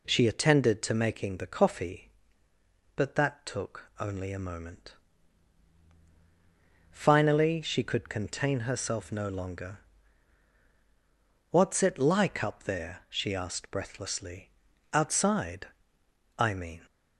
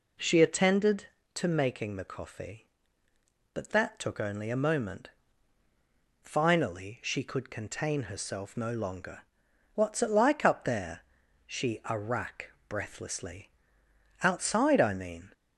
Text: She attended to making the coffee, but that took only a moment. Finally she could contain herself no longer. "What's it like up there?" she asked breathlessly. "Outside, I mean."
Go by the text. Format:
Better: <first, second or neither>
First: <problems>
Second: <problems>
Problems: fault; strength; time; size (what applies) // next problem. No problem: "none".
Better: first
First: none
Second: says "arrack" for "asked"; at 11.8 s